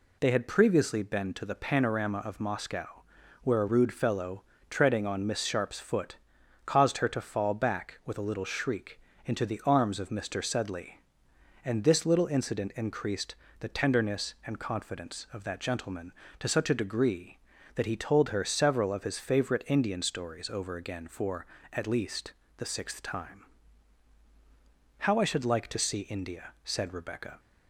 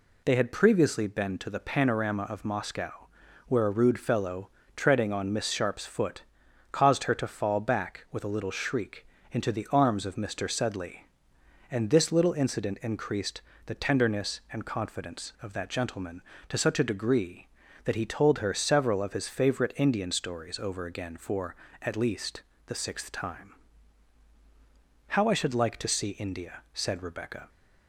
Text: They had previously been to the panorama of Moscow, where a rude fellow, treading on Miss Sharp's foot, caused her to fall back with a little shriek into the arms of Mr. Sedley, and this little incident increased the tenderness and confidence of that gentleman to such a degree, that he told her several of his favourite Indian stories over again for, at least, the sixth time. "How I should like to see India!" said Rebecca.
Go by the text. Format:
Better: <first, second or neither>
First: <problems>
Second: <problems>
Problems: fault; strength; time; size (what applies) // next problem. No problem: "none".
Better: neither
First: pauses between "shriek" and "into"; slight; at 8.9 s; 0.26 s long // pauses between "increased" and "the"; slight; at 13.3 s; 0.24 s long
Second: pauses between "shriek" and "into"; slight; at 9.0 s; 0.26 s long // pauses between "increased" and "the"; slight; at 13.4 s; 0.24 s long